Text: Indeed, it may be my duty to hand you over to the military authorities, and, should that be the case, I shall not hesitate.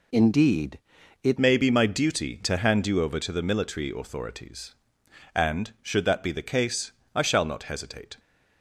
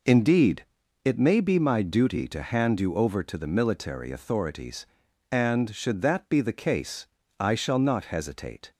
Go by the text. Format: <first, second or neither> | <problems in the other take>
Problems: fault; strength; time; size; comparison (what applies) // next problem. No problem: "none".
second | changes voice at "may"; from 1.3 s on; 6.8 s long